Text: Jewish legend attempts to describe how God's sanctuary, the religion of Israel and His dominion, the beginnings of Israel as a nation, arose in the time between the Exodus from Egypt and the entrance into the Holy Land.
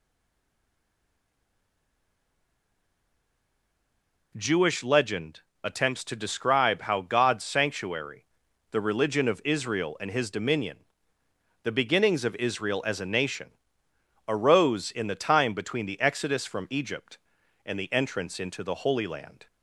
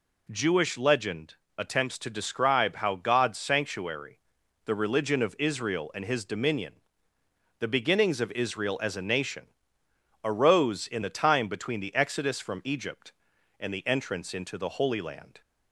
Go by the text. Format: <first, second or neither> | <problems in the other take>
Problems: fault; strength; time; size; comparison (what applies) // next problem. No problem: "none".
second | stays silent before the first word; strong; until 4.3 s; 4.3 s long // pauses between "legend" and "attempts"; slight; at 5.4 s; 0.22 s long; slight in the second